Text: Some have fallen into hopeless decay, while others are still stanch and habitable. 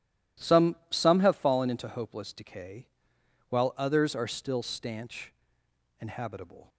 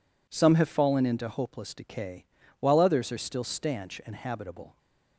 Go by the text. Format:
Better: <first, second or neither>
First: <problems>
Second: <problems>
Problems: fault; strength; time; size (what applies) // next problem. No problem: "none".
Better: second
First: says "Some" twice; at 0.8 s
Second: none